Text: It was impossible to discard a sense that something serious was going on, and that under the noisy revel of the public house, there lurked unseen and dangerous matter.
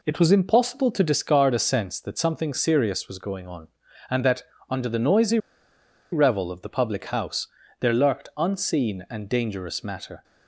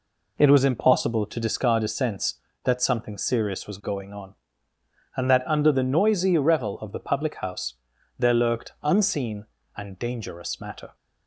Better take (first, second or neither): second